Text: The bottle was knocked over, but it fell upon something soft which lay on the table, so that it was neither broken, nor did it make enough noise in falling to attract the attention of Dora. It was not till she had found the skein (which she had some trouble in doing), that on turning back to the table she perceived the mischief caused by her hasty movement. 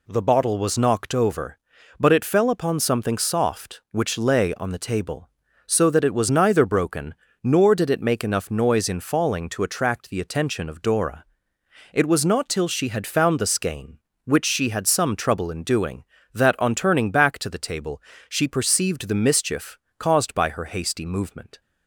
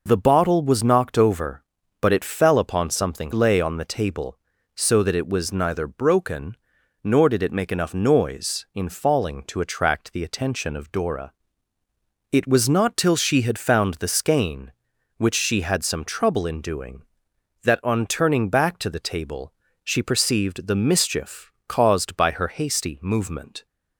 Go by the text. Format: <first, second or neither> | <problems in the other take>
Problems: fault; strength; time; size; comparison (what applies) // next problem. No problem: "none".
first | skips "soft which"; at 3.3 s // pauses between "table" and "she"; slight; at 19.5 s; 0.30 s long; slight in the first // pauses between "mischief" and "caused"; slight; at 21.5 s; 0.16 s long; slight in the first